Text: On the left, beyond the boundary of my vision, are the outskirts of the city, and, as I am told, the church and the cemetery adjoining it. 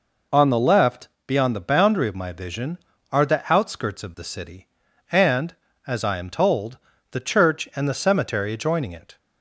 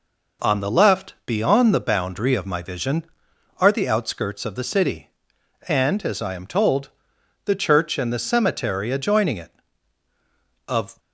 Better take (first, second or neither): first